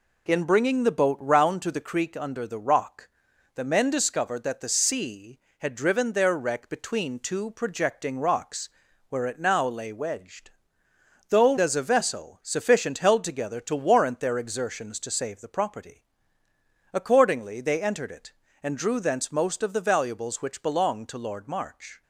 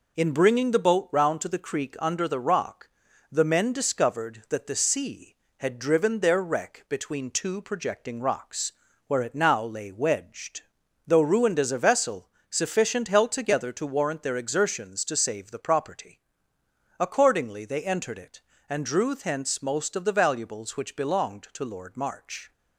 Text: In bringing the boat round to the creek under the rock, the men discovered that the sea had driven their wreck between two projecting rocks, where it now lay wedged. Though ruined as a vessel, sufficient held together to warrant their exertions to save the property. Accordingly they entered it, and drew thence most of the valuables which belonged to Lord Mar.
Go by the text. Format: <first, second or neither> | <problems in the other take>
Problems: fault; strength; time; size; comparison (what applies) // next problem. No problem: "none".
second | skips "ruined"; at 11.5 s